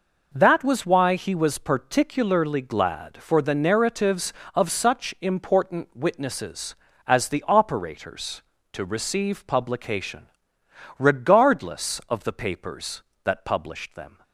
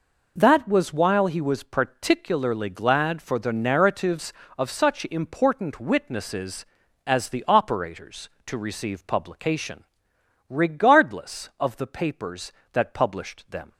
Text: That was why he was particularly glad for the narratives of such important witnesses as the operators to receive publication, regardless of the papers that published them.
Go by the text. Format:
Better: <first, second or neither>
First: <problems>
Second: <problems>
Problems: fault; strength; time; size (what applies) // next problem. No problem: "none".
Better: first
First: none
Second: says "while" for "why"; at 0.9 s